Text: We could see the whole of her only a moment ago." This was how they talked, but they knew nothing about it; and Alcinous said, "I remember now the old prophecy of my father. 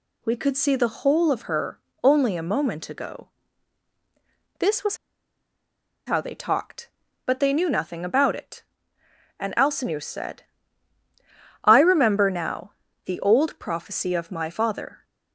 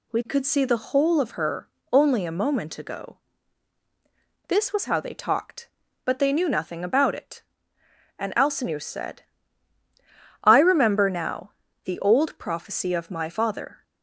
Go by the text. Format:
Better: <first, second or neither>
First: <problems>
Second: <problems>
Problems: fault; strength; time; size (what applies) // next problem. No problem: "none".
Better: second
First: pauses between "her" and "only"; slight; at 1.7 s; 0.24 s long // pauses between "was" and "how"; at 4.9 s; 1.1 s long // pauses between "now" and "the"; slight; at 12.7 s; 0.32 s long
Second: pauses between "her" and "only"; slight; at 1.6 s; 0.24 s long // pauses between "now" and "the"; slight; at 11.5 s; 0.32 s long